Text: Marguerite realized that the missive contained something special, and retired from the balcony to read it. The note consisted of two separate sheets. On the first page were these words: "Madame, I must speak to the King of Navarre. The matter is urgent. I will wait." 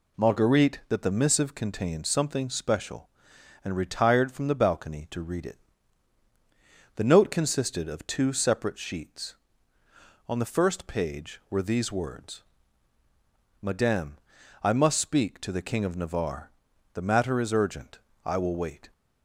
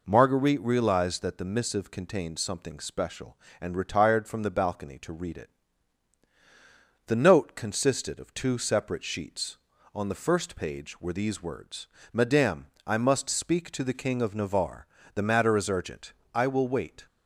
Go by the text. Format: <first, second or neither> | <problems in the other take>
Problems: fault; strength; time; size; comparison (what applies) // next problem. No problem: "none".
second | skips "realized"; at 0.8 s